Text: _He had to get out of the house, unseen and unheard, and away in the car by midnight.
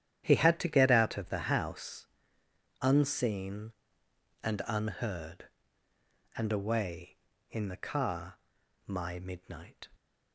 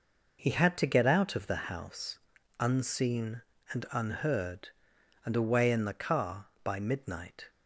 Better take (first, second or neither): second